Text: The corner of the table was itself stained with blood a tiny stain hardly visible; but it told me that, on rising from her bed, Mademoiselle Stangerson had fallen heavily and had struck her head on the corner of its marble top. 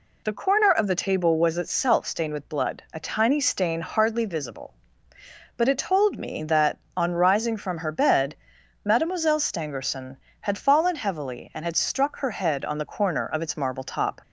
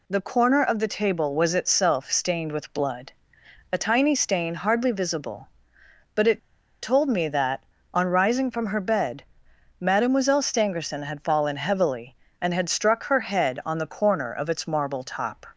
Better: first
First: none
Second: pauses between "blood" and "a"; noticeable; at 3.1 s; 0.60 s long // pauses between "it" and "told"; at 6.3 s; 0.45 s long

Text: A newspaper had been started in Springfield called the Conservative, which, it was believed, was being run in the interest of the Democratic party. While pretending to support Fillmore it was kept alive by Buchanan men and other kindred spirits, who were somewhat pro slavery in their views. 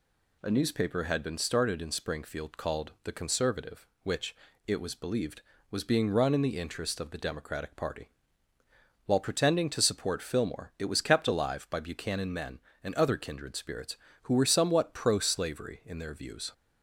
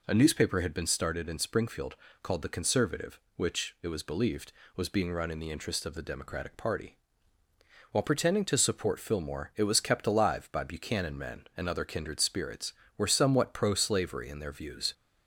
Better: first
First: none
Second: pauses between "Springfield" and "called"; slight; at 1.9 s; 0.28 s long // skips "who"; at 12.8 s

